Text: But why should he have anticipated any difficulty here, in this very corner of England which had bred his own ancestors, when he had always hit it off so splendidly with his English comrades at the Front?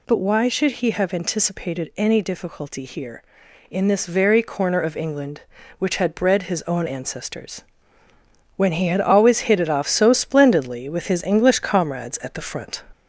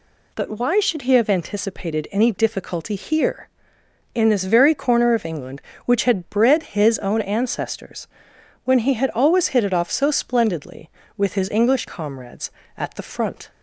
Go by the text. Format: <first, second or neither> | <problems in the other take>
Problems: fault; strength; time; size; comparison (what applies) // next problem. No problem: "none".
second | gets louder; slight; throughout; 2.5 dB